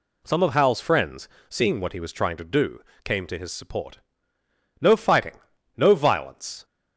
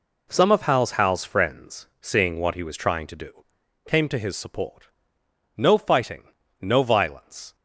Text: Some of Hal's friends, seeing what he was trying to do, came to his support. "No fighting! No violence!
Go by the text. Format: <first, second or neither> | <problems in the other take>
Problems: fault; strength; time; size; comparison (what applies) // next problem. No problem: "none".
first | says "Hal's" twice; at 0.9 s